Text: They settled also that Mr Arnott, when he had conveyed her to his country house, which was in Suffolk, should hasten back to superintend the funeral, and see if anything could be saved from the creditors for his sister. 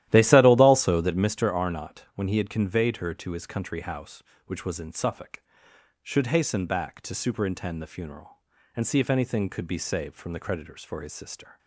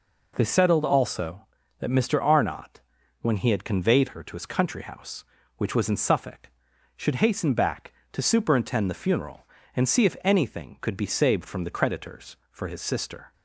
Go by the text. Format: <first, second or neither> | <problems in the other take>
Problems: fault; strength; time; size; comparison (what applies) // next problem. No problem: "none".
second | starts louder than the rest; strong; until 1.3 s; 13.5 dB